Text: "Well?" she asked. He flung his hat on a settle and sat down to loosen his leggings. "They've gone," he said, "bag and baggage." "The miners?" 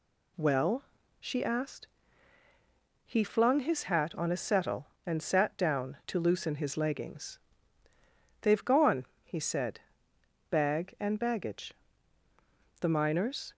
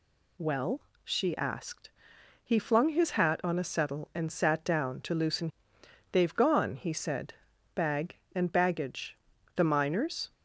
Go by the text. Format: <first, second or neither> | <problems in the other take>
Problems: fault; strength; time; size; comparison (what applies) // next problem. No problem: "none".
first | skips "his leggings"; at 5.7 s